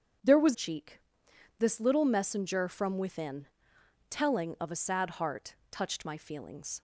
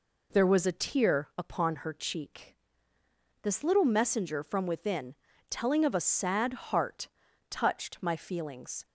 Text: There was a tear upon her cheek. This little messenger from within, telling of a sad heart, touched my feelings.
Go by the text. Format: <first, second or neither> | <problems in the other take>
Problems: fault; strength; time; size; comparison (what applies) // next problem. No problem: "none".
second | starts louder than the rest; strong; until 1.8 s; 7.5 dB // skips "a tear upon her"; at 0.5 s